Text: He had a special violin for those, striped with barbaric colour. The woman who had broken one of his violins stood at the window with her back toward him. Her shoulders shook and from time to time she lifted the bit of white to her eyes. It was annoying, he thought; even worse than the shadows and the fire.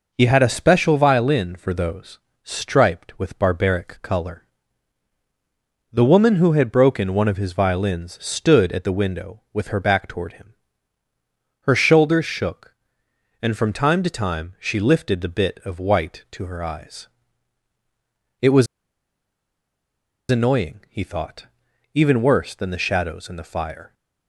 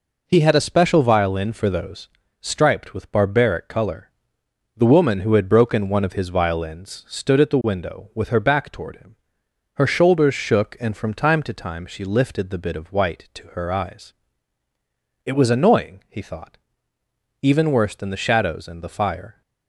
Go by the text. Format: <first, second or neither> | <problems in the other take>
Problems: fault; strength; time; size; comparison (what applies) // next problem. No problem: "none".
second | pauses between "was" and "annoying"; strong; at 18.6 s; 1.6 s long